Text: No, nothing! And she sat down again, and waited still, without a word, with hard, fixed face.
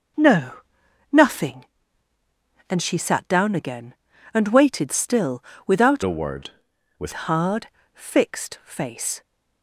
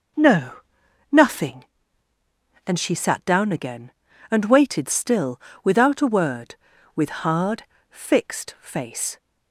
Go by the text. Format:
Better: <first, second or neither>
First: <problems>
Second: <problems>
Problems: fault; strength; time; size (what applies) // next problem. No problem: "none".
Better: second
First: changes voice from "a" to "with"; from 6.0 to 7.1 s; 1.1 s long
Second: none